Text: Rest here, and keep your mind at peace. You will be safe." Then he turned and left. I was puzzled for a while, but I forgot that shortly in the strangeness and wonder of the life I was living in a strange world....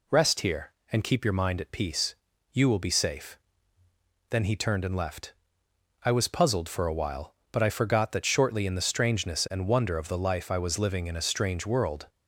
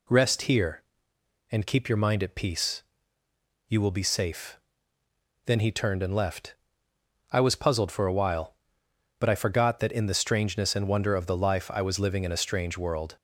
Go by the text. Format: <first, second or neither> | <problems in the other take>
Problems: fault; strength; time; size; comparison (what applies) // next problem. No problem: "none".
first | skips "shortly"; at 9.8 s